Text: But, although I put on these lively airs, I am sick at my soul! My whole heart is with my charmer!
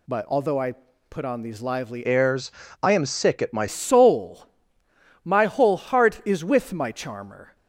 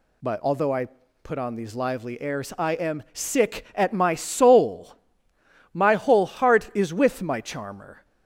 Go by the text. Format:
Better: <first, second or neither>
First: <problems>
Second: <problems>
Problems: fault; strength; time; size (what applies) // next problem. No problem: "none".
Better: second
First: pauses between "I" and "put"; slight; at 0.7 s; 0.36 s long // changes voice from "airs" to "my"; from 2.0 to 3.6 s; 1.6 s long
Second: pauses between "I" and "put"; slight; at 0.8 s; 0.36 s long